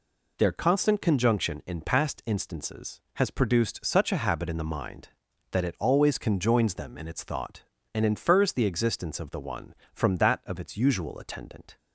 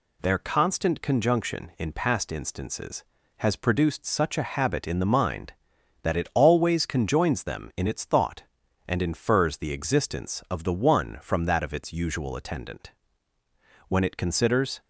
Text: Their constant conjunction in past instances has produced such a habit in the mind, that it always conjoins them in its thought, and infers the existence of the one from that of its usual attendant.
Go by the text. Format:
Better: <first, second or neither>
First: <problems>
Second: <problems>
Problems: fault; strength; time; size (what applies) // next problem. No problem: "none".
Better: first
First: none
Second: goes on to say "When it considers"; noticeable; from 13.8 s on; 0.92 s long